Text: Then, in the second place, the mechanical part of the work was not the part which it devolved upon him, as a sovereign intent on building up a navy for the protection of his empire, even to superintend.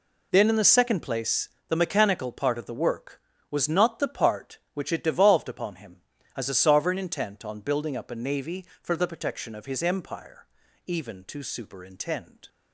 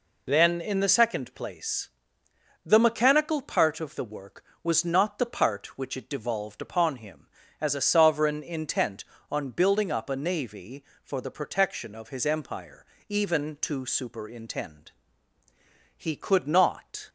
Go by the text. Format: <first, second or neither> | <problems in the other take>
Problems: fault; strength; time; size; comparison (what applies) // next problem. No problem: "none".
first | goes on to say "He could not"; noticeable; from 15.9 s on; 1.1 s long